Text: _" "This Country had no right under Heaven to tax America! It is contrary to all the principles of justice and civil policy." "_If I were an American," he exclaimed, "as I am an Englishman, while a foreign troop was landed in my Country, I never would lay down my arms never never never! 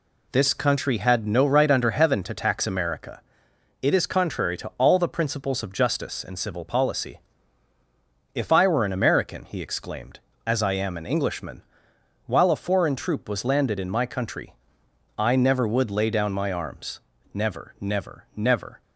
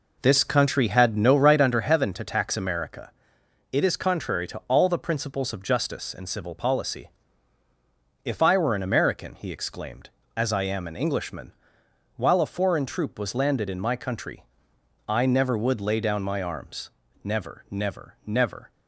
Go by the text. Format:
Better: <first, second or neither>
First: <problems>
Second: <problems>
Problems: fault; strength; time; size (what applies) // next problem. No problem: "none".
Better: first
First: pauses between "arms" and "never"; slight; at 16.9 s; 0.34 s long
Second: starts louder than the rest; noticeable; until 1.7 s; 4 dB // pauses between "arms" and "never"; slight; at 16.8 s; 0.34 s long